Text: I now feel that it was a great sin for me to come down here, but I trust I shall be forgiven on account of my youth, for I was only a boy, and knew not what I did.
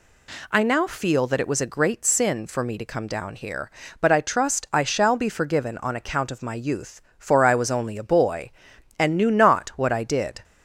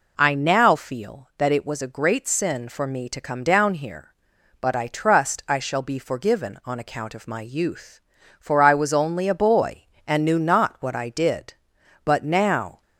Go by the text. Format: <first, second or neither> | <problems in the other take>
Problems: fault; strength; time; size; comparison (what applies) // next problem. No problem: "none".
first | goes on to say "But now"; noticeable; from 12.0 s on; 0.76 s long